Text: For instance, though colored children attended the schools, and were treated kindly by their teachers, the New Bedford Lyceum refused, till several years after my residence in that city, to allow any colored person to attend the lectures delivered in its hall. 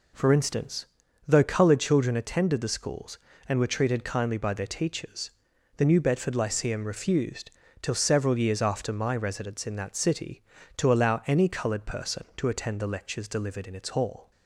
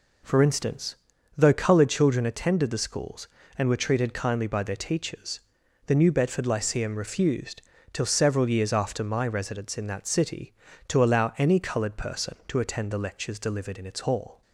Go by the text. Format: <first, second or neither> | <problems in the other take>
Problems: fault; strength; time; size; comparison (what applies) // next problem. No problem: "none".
neither | none